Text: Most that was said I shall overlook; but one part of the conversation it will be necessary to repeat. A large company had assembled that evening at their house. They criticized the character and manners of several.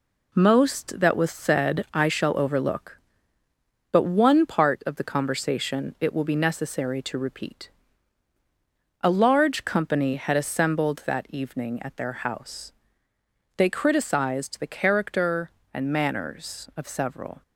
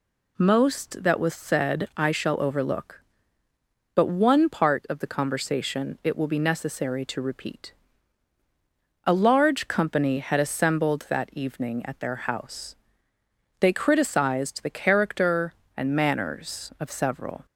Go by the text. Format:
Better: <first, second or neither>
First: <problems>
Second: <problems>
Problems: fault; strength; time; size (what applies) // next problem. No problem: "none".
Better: second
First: gets quieter; noticeable; throughout; 6 dB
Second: none